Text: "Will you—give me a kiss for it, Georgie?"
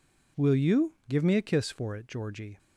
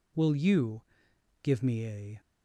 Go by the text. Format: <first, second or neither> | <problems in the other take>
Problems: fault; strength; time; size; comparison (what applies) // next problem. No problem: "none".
first | stops before "kiss for it Georgie"; at 2.1 s